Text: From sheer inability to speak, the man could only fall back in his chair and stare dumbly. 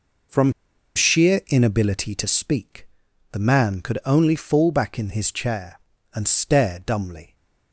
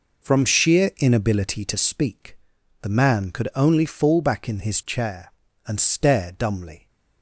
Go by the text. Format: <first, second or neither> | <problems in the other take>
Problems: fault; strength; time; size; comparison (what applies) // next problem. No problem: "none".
second | pauses between "From" and "sheer"; at 0.5 s; 0.43 s long